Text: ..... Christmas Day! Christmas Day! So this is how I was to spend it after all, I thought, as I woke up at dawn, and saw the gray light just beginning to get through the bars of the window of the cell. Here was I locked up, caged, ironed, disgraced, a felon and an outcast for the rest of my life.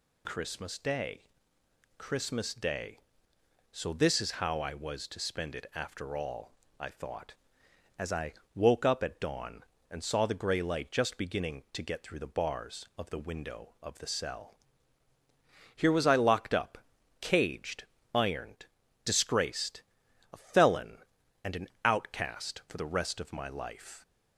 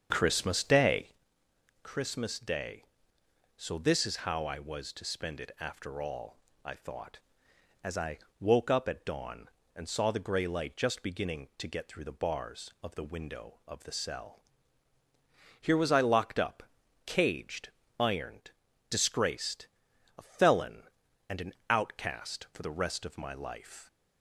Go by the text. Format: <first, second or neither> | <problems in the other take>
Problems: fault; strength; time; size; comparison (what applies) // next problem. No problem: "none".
first | starts louder than the rest; strong; until 1.2 s; 7 dB // pauses between "I" and "woke"; slight; at 8.1 s; 0.20 s long; slight in the first // pauses between "an" and "outcast"; slight; at 21.5 s; 0.16 s long; slight in the first